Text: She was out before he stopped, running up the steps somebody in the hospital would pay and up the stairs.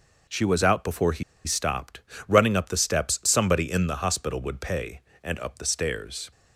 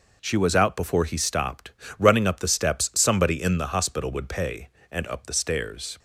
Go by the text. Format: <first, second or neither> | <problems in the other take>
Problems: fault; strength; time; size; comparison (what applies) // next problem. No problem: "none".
second | pauses between "he" and "stopped"; slight; at 1.2 s; 0.23 s long